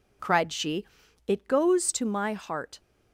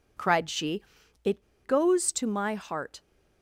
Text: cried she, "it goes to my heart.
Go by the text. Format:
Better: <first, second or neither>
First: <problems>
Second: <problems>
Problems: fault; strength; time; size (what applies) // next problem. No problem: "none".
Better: first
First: none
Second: pauses between "it" and "goes"; slight; at 1.4 s; 0.23 s long